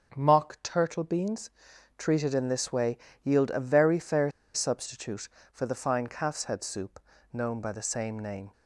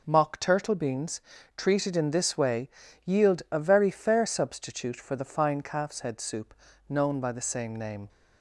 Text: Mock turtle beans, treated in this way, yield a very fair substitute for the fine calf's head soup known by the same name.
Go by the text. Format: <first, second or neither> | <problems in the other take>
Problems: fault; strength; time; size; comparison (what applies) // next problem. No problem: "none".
second | starts louder than the rest; strong; until 1.2 s; 7 dB // pauses between "fair" and "substitute"; slight; at 4.3 s; 0.23 s long // pauses between "soup" and "known"; slight; at 6.9 s; 0.32 s long; slight in the second